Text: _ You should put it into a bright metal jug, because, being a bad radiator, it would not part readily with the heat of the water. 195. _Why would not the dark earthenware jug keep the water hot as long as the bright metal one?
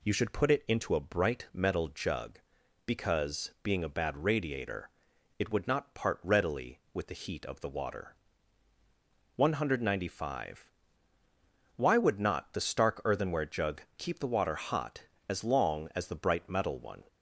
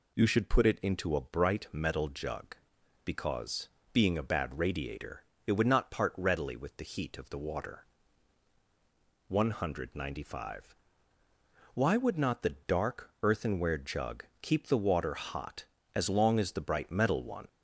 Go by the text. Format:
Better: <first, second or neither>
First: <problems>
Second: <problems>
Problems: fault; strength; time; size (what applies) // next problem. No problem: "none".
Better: second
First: says "stark" for "dark"; at 12.5 s // pauses between "jug" and "keep"; slight; at 13.8 s; 0.16 s long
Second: pauses between "jug" and "keep"; slight; at 14.2 s; 0.18 s long